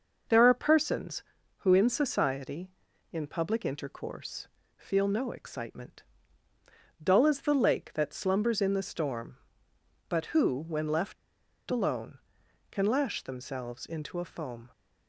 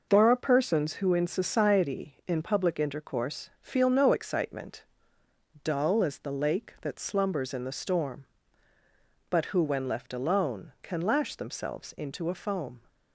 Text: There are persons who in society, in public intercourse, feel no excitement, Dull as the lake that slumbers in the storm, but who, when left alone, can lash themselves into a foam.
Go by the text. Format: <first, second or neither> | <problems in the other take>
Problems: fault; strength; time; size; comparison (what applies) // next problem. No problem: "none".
second | pauses between "left" and "alone"; noticeable; at 11.1 s; 0.53 s long